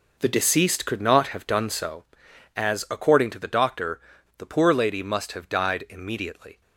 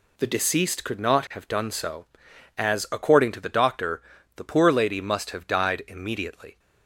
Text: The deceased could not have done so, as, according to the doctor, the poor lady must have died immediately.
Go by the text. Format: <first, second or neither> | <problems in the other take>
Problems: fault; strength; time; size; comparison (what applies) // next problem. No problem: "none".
second | starts louder than the rest; noticeable; until 1.9 s; 5 dB